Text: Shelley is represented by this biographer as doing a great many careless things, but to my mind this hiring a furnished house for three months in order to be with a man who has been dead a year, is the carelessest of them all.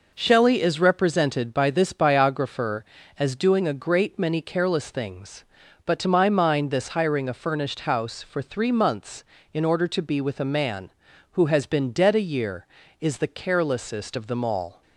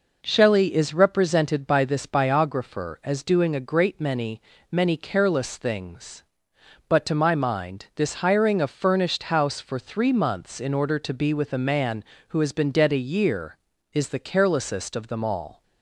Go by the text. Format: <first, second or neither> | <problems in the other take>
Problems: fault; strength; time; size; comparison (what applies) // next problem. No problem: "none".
first | says "many" twice; at 4.6 s